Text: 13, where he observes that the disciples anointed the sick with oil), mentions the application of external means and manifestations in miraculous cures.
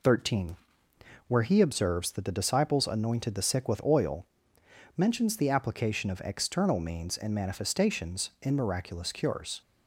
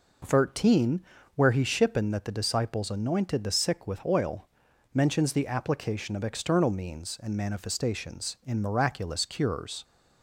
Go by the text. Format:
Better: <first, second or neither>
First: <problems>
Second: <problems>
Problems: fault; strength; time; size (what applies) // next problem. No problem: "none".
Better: first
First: none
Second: says "shippen" for "observes"; at 1.6 s